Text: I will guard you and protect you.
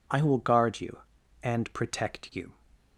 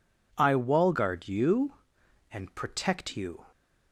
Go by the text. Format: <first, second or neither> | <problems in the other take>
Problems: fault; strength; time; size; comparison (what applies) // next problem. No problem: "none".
first | says "wall" for "will"; at 0.5 s